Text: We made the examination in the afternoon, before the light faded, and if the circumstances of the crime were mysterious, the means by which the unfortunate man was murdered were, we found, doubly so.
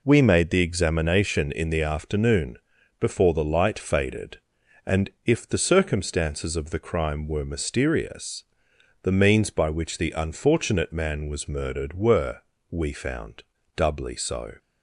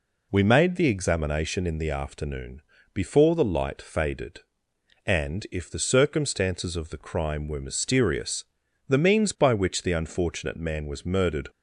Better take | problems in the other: first | stops before "were we found doubly so"; at 11.4 s

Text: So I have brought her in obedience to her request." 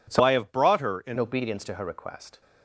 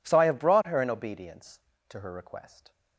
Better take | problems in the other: second | changes voice from "I" to "in"; from 0.2 to 1.1 s; 0.9 s long

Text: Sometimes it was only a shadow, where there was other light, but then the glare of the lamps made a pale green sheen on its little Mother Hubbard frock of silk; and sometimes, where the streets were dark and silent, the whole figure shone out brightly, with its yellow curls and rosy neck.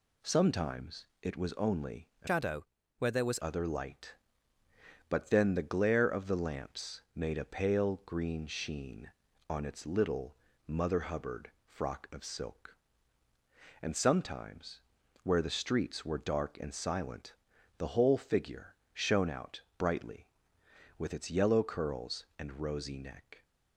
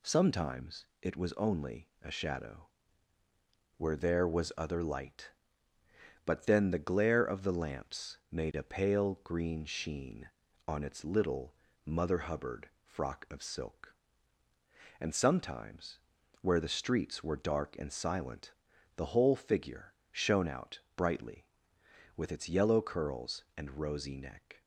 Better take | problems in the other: second | pauses between "Sometimes" and "it"; slight; at 1.0 s; 0.16 s long; slight in the second // changes voice from "shadow" to "was"; from 2.2 to 3.4 s; 1.2 s long // pauses between "little" and "Mother"; slight; at 10.3 s; 0.30 s long; slight in the second // pauses between "figure" and "shone"; slight; at 18.7 s; 0.16 s long; slight in the second // pauses between "out" and "brightly"; slight; at 19.6 s; 0.16 s long; slight in the second

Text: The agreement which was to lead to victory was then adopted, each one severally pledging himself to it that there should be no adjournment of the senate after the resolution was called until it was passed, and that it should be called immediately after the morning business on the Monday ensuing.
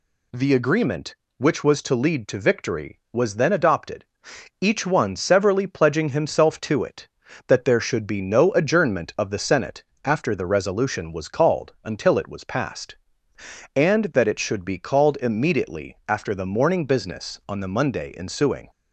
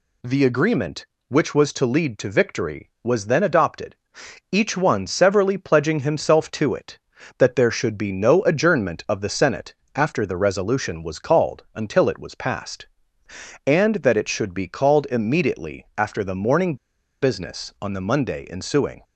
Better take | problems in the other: first | pauses between "senate" and "after"; slight; at 9.7 s; 0.22 s long; slight in the first // pauses between "morning" and "business"; noticeable; at 16.7 s; 0.46 s long

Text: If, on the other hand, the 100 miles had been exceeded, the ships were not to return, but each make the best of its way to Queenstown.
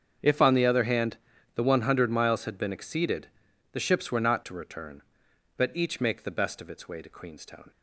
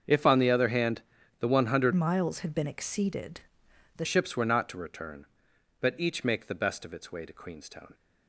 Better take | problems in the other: first | starts louder than the rest; until 1.4 s; 6.5 dB; strong in the first // changes voice from "miles" to "the"; from 1.9 to 4.0 s; 2.1 s long

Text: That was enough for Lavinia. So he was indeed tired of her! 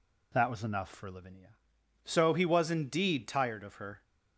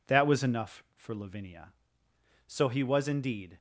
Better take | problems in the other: first | stops before "tired of her"; at 3.5 s

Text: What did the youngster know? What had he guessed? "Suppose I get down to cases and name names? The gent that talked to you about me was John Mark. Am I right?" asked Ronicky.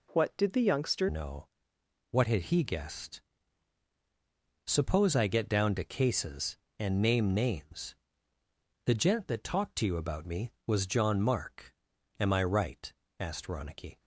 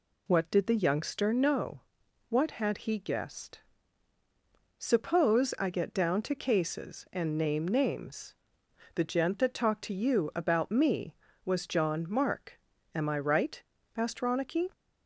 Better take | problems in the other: second | changes voice at "know"; from 1.0 s on; 12.9 s long

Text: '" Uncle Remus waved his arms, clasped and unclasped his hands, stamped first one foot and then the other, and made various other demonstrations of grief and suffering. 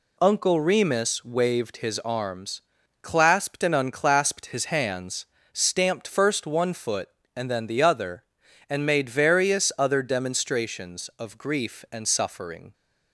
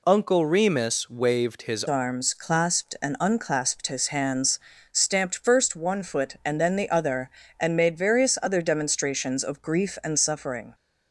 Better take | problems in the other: first | changes voice at "arms"; from 1.8 s on; 8.9 s long

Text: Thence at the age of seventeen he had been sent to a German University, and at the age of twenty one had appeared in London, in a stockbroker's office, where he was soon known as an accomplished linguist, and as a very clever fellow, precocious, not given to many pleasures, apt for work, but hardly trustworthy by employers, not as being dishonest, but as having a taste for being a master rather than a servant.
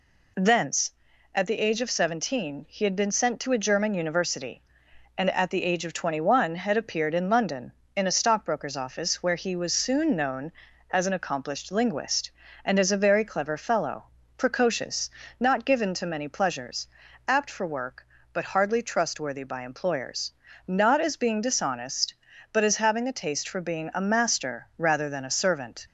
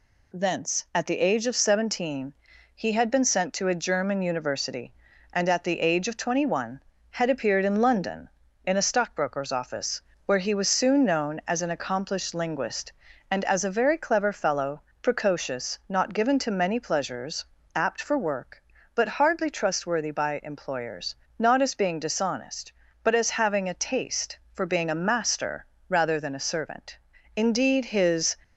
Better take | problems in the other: first | pauses between "seventeen" and "he"; at 2.3 s; 0.42 s long // pauses between "master" and "rather"; slight; at 25.6 s; 0.24 s long // goes on to say "Indeed his"; noticeable; from 27.3 s on; 1.0 s long

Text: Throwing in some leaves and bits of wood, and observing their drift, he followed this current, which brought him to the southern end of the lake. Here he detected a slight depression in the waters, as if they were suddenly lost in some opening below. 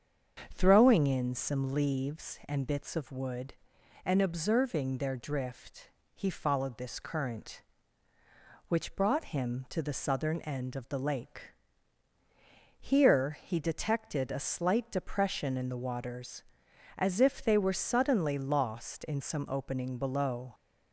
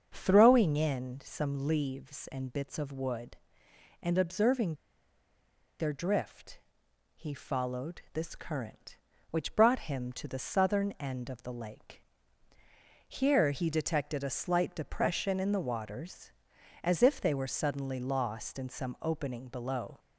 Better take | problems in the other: first | starts louder than the rest; until 1.1 s; 6.5 dB; strong in the first // pauses between "observing" and "their"; at 4.7 s; 1.0 s long

